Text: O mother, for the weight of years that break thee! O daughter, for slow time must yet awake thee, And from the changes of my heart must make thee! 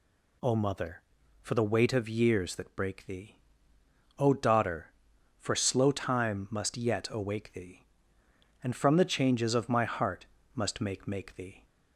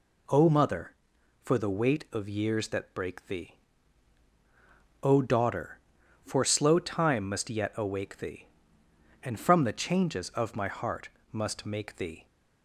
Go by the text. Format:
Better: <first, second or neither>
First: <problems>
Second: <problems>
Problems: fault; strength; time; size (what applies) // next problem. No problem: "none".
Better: second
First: pauses between "heart" and "must"; slight; at 10.2 s; 0.28 s long // says "make" twice; at 11.0 s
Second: pauses between "heart" and "must"; slight; at 11.0 s; 0.24 s long